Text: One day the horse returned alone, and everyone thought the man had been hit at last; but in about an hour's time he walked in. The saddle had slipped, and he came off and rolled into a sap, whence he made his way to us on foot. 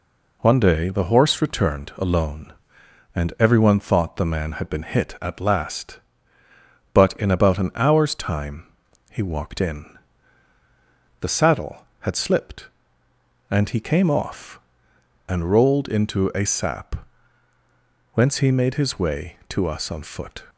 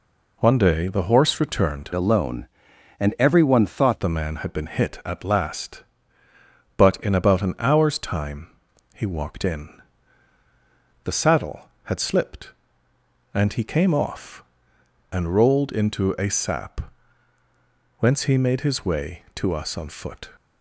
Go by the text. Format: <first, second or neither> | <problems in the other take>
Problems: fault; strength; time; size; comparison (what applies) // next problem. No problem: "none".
first | changes voice from "alone" to "thought"; from 1.9 to 4.0 s; 2.1 s long // pauses between "time" and "he"; noticeable; at 8.4 s; 0.48 s long; noticeable in the first